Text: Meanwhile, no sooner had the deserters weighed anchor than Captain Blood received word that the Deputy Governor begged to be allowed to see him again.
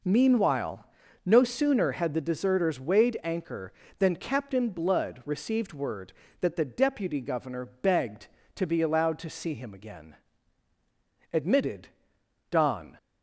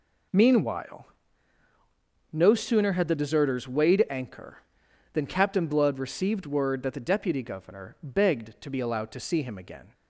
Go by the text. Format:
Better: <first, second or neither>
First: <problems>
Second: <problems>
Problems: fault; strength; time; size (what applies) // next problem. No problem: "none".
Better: second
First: goes on to say "Admitted Don"; from 11.3 s on; 1.6 s long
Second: none